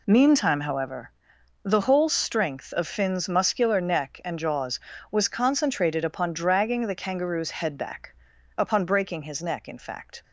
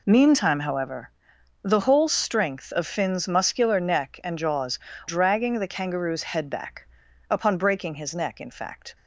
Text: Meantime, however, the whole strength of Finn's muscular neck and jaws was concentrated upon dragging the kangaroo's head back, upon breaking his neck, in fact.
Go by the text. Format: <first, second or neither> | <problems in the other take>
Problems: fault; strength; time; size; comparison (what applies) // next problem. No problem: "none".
first | skips "was concentrated upon"; at 4.9 s